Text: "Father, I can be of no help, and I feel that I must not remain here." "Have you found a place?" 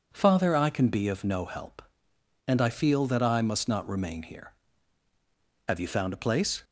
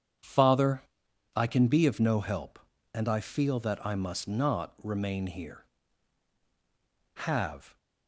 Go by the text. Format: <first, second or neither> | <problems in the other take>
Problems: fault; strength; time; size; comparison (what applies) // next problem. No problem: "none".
first | starts louder than the rest; strong; until 1.7 s; 8 dB // stops before "you found a place"; at 7.7 s